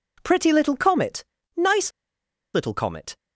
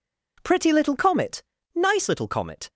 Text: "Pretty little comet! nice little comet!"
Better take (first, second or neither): second